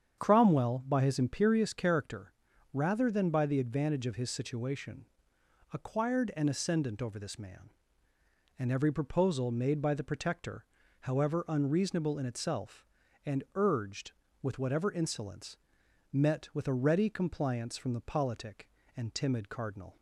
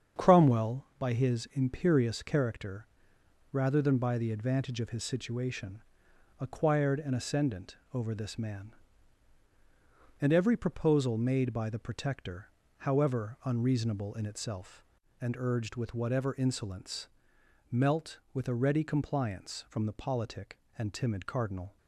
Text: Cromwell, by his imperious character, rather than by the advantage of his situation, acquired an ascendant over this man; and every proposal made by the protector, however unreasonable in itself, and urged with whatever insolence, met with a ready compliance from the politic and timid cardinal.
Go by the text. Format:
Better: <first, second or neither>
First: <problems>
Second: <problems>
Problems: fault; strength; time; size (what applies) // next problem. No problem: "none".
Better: first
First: starts louder than the rest; strong; until 1.2 s; 8 dB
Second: starts louder than the rest; strong; until 1.2 s; 7.5 dB // pauses between "ascendant" and "over"; slight; at 7.7 s; 0.16 s long // says "melt" for "met"; at 17.7 s